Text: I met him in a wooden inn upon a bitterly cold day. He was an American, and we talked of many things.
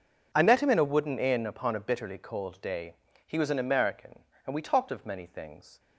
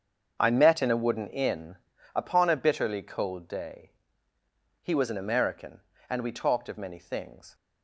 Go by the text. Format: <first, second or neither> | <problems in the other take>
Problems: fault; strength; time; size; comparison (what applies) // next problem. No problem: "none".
first | starts louder than the rest; until 1.4 s; 7 dB // skips "him"; at 0.8 s // pauses between "inn" and "upon"; slight; at 1.7 s; 0.36 s long